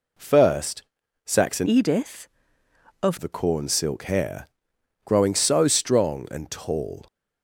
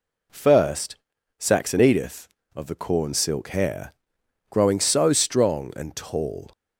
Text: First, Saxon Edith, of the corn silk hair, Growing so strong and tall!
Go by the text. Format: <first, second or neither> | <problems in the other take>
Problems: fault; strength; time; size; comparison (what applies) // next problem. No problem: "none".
second | changes voice from "Edith" to "of"; from 1.6 to 3.1 s; 1.5 s long